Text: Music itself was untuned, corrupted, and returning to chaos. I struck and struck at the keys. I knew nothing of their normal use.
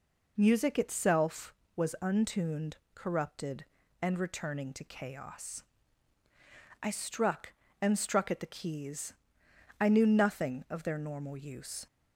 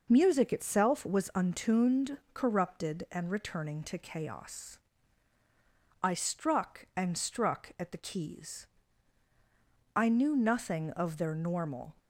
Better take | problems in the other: first | stops before "use"; at 11.9 s

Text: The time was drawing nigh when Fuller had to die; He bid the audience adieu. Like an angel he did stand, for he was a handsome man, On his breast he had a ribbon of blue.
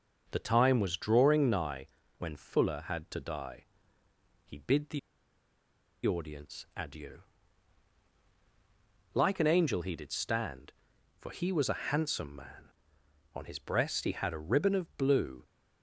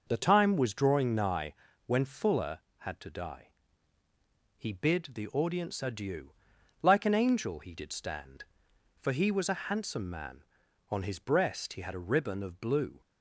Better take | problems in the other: second | starts louder than the rest; until 1.3 s; 6.5 dB // pauses between "nigh" and "when"; slight; at 1.8 s; 0.30 s long; slight in the second // pauses between "the" and "audience"; at 4.9 s; 1.0 s long

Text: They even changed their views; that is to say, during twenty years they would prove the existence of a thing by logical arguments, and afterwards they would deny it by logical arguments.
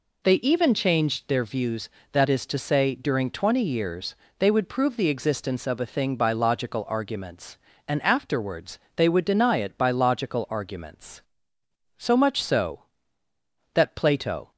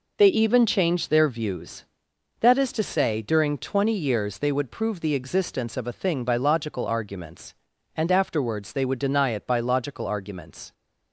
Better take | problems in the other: second | pauses between "years" and "they"; slight; at 4.1 s; 0.22 s long // pauses between "afterwards" and "they"; slight; at 8.7 s; 0.20 s long // goes on to say "So much so that Plato"; strong; from 11.9 s on; 2.5 s long

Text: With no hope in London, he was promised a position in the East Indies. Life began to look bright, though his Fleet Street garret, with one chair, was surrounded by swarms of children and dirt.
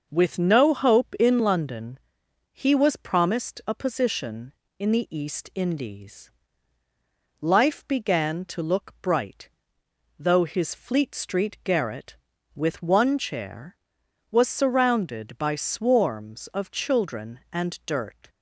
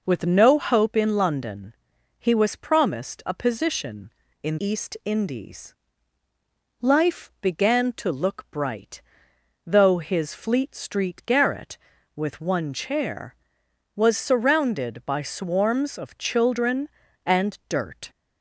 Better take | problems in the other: first | skips "the"; at 4.5 s

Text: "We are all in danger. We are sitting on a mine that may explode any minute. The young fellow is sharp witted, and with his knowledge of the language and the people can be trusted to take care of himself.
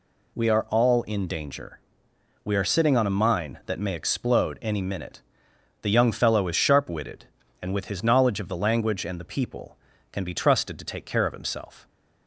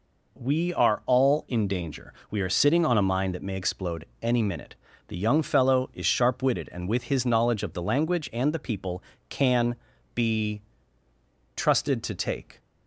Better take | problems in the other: first | pauses between "explode" and "any"; slight; at 4.0 s; 0.16 s long // pauses between "can" and "be"; at 9.7 s; 0.42 s long // pauses between "be" and "trusted"; noticeable; at 10.6 s; 0.94 s long // stops before "care of himself"; at 12.5 s

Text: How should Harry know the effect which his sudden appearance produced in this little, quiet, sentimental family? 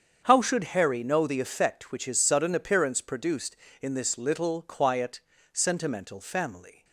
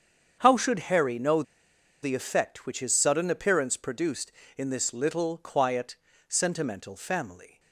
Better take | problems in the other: first | starts louder than the rest; strong; until 1.4 s; 7.5 dB; strong in the first // pauses between "know" and "the"; noticeable; at 1.4 s; 0.60 s long

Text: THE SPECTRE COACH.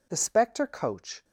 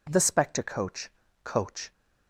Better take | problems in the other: first | says "COACH" twice; at 1.4 s

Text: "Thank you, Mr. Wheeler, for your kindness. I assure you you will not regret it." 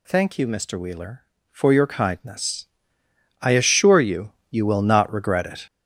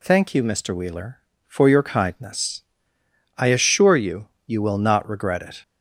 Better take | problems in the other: second | gets louder; strong; throughout; 8 dB // pauses between "you" and "you"; slight; at 4.3 s; 0.18 s long; slight in the second

